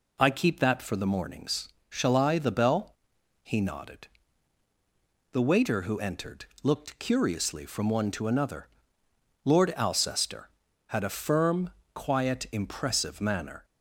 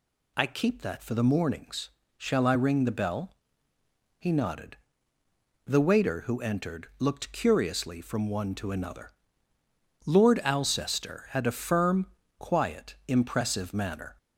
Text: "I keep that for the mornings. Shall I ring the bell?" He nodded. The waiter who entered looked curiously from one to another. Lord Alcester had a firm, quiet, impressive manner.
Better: second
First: skips "ring"; at 2.3 s // pauses between "entered" and "looked"; slight; at 6.4 s; 0.18 s long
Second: none

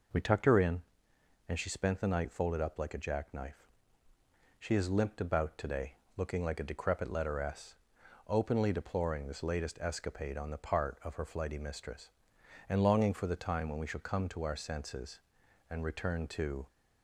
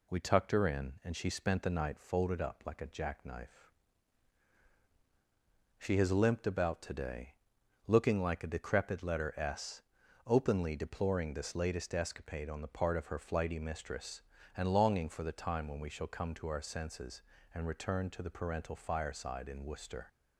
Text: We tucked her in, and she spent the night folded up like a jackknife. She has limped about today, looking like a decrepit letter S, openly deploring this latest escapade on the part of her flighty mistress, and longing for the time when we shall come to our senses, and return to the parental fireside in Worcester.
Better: second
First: stops before "the parental fireside in Worcester"; at 16.6 s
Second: none

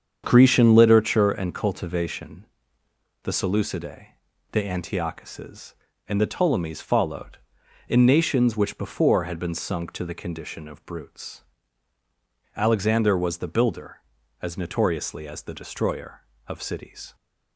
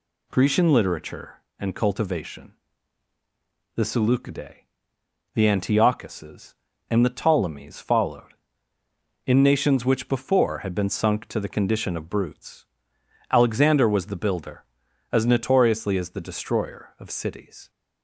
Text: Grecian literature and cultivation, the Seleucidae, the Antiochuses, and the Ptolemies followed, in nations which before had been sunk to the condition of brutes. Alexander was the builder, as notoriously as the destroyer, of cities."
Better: second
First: starts louder than the rest; strong; until 1.3 s; 7.5 dB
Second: none

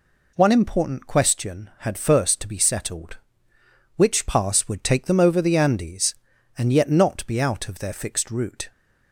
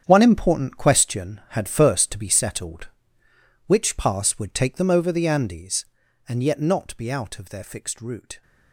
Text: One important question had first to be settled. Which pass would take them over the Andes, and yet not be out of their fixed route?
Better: first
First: none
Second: gets quieter; strong; throughout; 12.5 dB

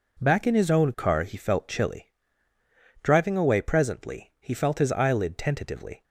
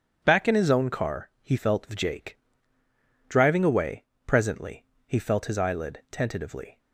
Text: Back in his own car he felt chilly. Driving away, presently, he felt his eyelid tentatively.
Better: first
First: none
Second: says "vjake" for "chilly"; at 1.8 s

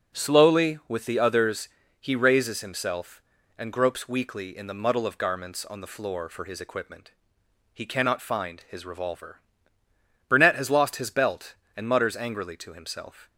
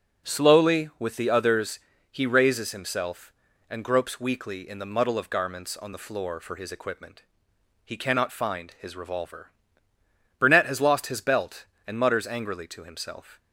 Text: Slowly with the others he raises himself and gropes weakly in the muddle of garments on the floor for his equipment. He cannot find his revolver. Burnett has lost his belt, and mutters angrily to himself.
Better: neither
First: pauses between "others" and "he"; slight; at 1.6 s; 0.32 s long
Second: pauses between "others" and "he"; slight; at 1.7 s; 0.32 s long

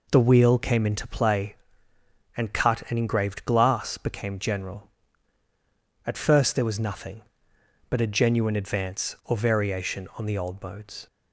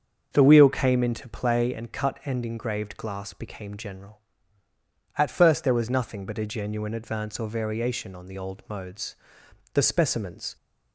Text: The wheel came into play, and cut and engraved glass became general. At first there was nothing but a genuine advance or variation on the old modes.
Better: first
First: none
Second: starts louder than the rest; until 1.3 s; 6.5 dB // goes on to say "The specimens"; noticeable; from 9.7 s on; 0.82 s long

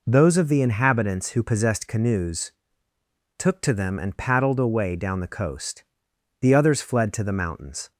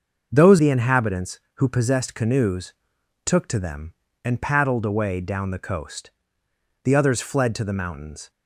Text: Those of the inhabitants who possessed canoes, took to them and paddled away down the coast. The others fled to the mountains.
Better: first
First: none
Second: starts louder than the rest; noticeable; until 1.3 s; 6 dB // skips "of"; at 0.5 s

